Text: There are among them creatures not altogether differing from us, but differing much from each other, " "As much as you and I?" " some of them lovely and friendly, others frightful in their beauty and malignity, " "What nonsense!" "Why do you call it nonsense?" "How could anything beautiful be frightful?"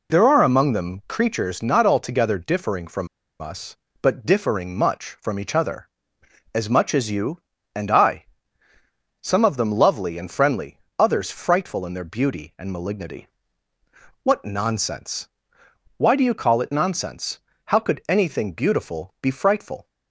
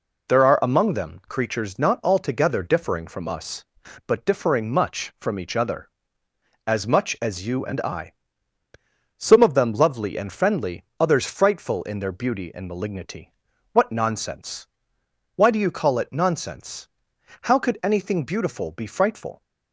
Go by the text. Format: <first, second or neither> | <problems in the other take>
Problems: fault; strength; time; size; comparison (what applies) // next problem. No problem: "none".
second | pauses between "from" and "us"; slight; at 3.0 s; 0.33 s long